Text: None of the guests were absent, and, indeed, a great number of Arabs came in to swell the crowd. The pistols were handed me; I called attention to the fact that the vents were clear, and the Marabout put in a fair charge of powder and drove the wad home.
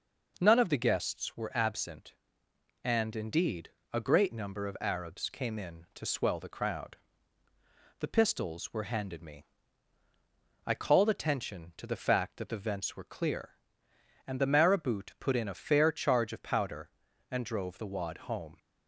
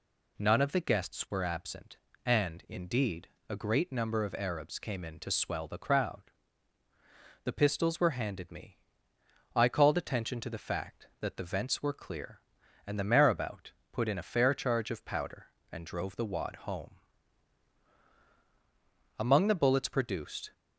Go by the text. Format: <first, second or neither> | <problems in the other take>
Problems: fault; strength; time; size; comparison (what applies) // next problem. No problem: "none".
first | pauses between "Marabout" and "put"; slight; at 13.7 s; 0.18 s long // goes on to say "Among the bullets produced"; from 19.1 s on; 1.3 s long